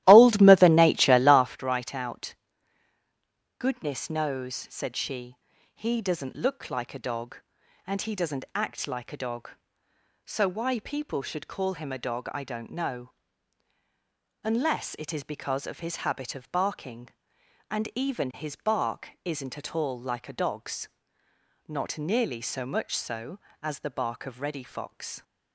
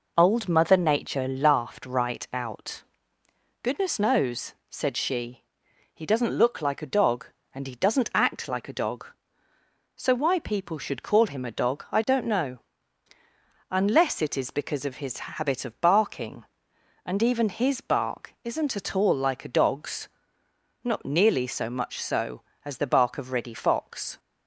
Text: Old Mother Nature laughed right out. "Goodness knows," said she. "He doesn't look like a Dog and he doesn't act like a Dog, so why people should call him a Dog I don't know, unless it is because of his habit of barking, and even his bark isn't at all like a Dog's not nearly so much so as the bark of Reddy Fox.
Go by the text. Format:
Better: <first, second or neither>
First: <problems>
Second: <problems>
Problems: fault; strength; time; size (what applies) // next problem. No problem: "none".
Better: second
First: starts louder than the rest; strong; until 1.6 s; 14.5 dB // pauses between "bark" and "isn't"; slight; at 19.0 s; 0.16 s long // pauses between "Dog's" and "not"; noticeable; at 20.8 s; 0.80 s long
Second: pauses between "Dog's" and "not"; noticeable; at 20.0 s; 0.76 s long